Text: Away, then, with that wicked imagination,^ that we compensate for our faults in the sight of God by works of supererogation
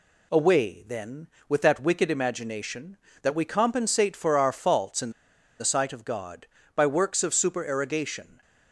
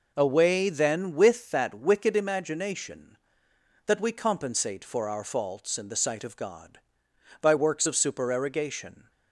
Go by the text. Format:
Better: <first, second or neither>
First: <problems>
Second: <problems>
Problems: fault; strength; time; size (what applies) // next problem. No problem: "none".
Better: second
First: pauses between "in" and "the"; noticeable; at 5.1 s; 0.47 s long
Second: none